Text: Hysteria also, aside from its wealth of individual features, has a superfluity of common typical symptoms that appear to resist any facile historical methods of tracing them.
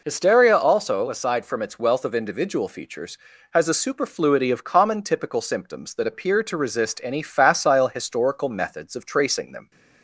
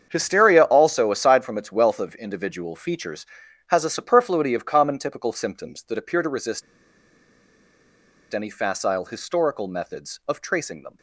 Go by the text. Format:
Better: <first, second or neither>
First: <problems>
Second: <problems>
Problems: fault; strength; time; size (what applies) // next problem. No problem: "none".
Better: first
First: none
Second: starts louder than the rest; strong; until 1.1 s; 7.5 dB // pauses between "resist" and "any"; strong; at 6.6 s; 1.7 s long